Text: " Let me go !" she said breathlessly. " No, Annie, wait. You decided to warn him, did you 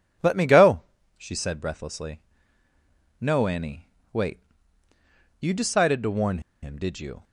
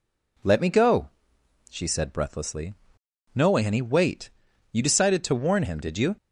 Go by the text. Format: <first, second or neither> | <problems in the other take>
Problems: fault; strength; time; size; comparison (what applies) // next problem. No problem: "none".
second | pauses between "warn" and "him"; slight; at 6.3 s; 0.23 s long